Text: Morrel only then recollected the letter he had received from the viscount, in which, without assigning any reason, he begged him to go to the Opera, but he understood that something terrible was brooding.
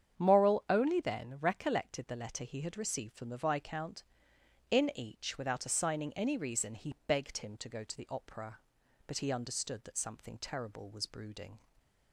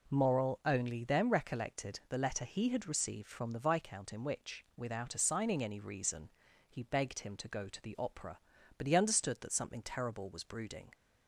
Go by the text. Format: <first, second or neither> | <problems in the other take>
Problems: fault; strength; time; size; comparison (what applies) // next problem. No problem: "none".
second | starts louder than the rest; strong; until 1.2 s; 8 dB // says "each" for "which"; at 4.9 s